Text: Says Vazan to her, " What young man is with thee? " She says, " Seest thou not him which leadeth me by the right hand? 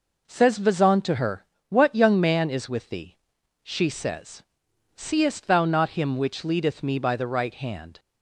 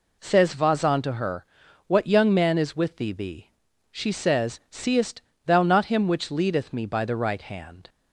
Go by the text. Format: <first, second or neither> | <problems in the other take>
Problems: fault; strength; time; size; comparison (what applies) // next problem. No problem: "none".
first | says "thee" twice; at 3.1 s // pauses between "Seest" and "thou"; slight; at 5.2 s; 0.24 s long